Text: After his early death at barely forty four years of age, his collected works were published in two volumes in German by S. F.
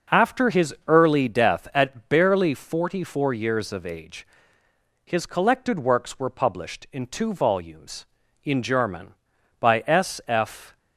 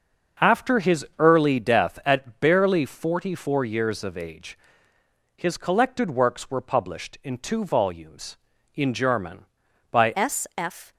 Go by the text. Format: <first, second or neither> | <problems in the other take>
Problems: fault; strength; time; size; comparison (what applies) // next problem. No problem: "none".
first | starts louder than the rest; until 1.5 s; 6.5 dB // changes voice at "S"; from 10.1 s on; 0.8 s long